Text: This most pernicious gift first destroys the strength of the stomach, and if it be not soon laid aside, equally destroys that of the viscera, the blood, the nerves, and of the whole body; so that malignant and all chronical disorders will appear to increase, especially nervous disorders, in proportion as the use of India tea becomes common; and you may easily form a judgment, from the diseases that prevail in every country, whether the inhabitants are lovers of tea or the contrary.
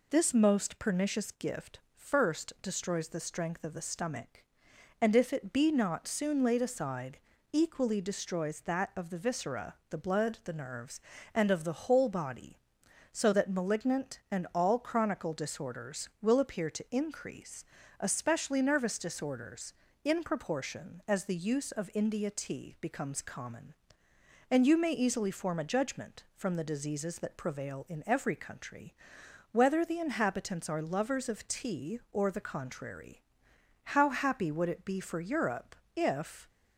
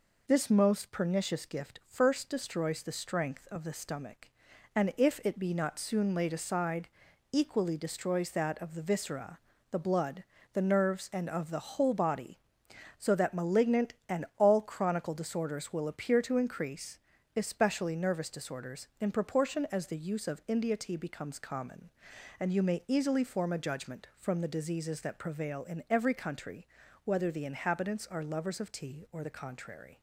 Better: second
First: pauses between "gift" and "first"; slight; at 1.7 s; 0.16 s long // goes on to say "How happy would it be for Europe if"; strong; from 33.8 s on; 2.6 s long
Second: none

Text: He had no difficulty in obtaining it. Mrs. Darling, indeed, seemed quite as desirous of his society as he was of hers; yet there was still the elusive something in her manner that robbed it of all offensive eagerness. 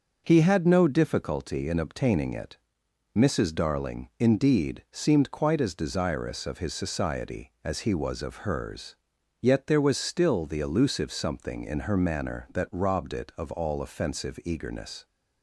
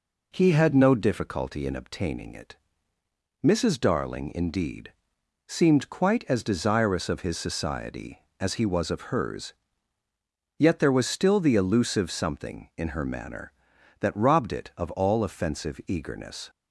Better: neither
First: none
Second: none

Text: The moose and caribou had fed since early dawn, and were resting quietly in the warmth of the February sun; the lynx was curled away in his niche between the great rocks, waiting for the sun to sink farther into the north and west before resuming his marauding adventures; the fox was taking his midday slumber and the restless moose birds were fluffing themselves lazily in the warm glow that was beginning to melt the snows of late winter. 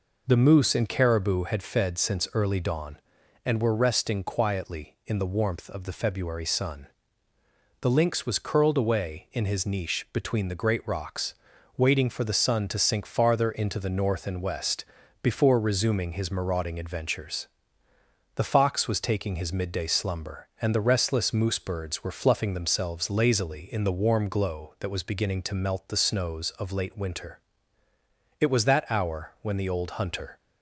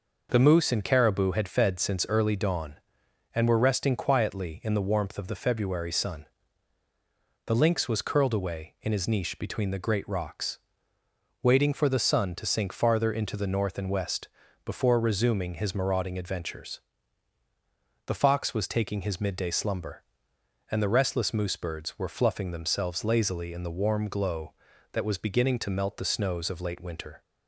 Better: second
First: pauses between "west" and "before"; at 14.8 s; 0.38 s long // goes on to say "It was that hour when the old hunter"; strong; from 28.3 s on; 1.9 s long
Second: pauses between "west" and "before"; slight; at 14.2 s; 0.36 s long

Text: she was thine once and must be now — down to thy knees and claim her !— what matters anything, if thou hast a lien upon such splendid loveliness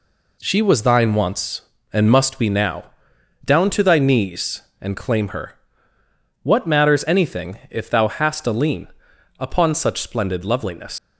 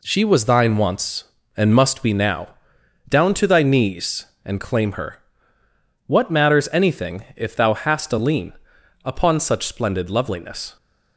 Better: second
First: pauses between "lien" and "upon"; noticeable; at 8.8 s; 0.50 s long // leaves "loveliness" unfinished; at 10.9 s; 125 ms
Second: pauses between "lien" and "upon"; noticeable; at 8.5 s; 0.50 s long

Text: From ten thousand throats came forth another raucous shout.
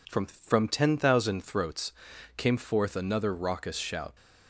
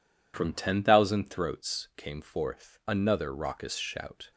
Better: second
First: says "From" twice; at 0.2 s // pauses between "throats" and "came"; noticeable; at 1.9 s; 0.46 s long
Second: none

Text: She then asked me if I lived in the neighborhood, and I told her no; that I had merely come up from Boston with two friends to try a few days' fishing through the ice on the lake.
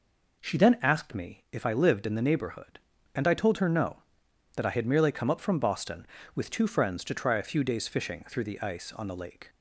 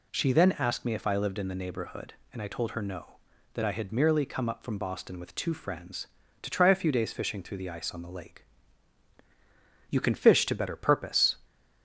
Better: first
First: none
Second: goes on to say "You can fish to better purpose"; from 9.8 s on; 1.4 s long

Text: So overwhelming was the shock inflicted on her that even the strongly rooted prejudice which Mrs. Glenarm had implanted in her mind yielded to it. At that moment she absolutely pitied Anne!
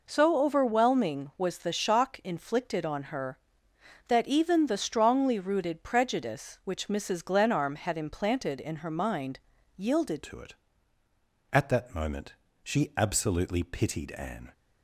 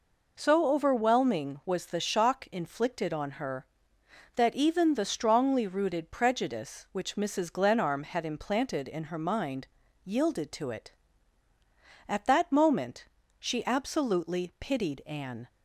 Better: second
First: pauses between "mind" and "yielded"; slight; at 9.3 s; 0.36 s long // changes voice at "to"; from 10.2 s on; 4.3 s long // pauses between "moment" and "she"; slight; at 12.3 s; 0.28 s long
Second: pauses between "mind" and "yielded"; slight; at 9.6 s; 0.36 s long // pauses between "moment" and "she"; slight; at 13.0 s; 0.32 s long

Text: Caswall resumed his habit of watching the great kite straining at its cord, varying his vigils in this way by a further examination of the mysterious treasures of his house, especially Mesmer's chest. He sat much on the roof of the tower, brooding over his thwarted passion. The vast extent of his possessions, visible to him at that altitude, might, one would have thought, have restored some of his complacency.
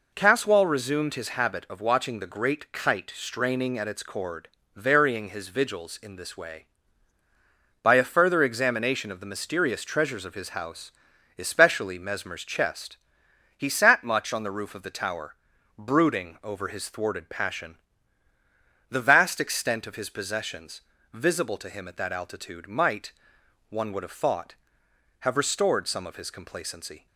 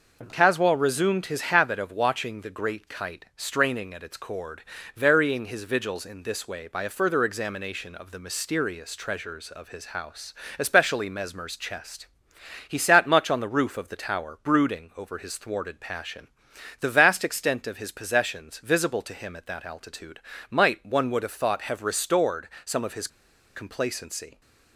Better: first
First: none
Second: pauses between "restored" and "some"; slight; at 22.4 s; 0.18 s long // pauses between "his" and "complacency"; noticeable; at 23.0 s; 0.47 s long

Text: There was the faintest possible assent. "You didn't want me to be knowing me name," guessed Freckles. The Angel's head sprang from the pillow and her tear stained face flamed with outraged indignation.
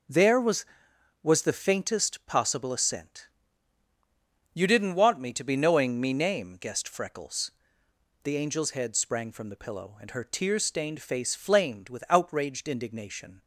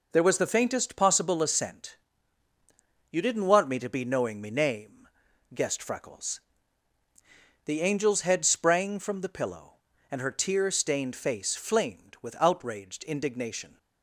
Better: second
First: says "was" twice; at 1.2 s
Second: none

